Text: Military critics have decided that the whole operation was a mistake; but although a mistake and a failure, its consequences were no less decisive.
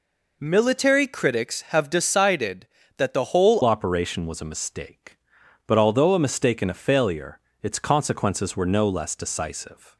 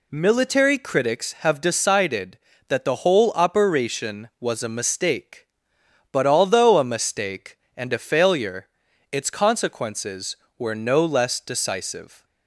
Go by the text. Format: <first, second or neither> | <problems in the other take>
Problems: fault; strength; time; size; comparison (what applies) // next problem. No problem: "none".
second | changes voice at "operation"; from 3.6 s on; 6.3 s long